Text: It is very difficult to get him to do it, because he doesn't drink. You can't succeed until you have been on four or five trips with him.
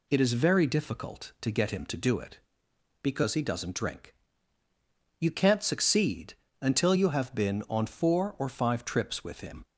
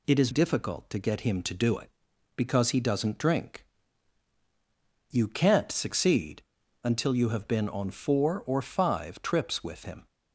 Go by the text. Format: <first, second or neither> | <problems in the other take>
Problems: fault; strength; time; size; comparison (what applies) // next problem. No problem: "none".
first | skips "very"; at 0.2 s // pauses between "succeed" and "until"; at 6.4 s; 0.42 s long; slight in the first